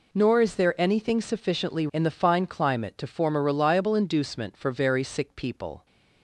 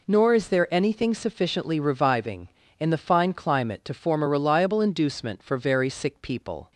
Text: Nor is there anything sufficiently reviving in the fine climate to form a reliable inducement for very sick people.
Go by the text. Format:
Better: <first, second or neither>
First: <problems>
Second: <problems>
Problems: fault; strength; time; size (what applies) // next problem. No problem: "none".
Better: second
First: skips "reviving"; at 1.8 s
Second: none